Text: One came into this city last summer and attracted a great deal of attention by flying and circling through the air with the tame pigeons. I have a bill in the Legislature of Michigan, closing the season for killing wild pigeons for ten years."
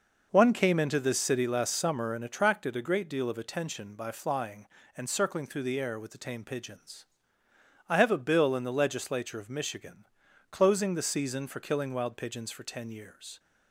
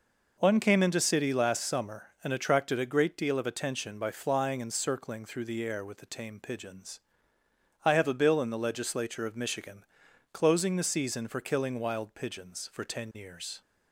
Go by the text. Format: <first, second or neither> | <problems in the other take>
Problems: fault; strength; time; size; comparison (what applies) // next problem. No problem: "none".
first | skips "this"; at 0.9 s